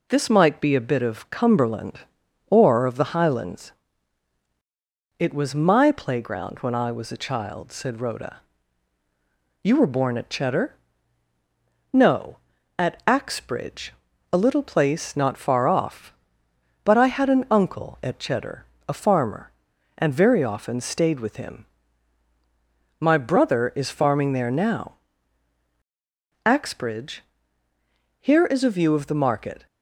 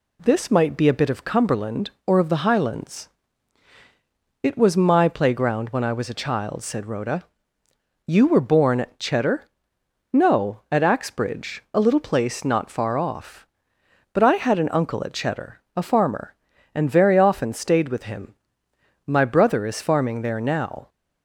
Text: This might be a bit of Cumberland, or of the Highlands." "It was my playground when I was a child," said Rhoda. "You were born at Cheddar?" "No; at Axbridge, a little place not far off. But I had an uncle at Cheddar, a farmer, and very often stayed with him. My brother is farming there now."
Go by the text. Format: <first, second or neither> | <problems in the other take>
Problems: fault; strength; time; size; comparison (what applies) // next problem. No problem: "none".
second | goes on to say "Axbridge Here is a view of the market"; strong; from 26.4 s on; 3.2 s long